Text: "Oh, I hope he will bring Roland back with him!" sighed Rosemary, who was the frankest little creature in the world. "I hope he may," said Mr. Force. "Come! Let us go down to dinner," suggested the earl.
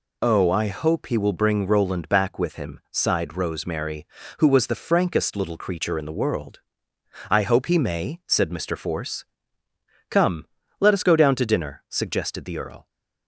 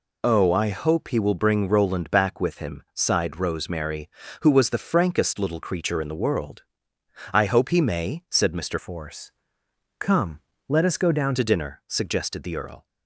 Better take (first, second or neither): first